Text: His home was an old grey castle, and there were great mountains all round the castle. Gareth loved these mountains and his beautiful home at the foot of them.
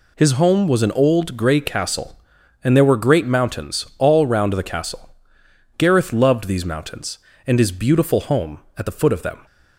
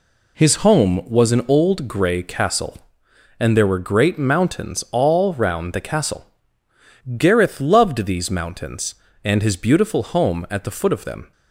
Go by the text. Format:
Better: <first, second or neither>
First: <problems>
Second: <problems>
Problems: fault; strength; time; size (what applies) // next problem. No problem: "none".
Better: neither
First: none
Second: none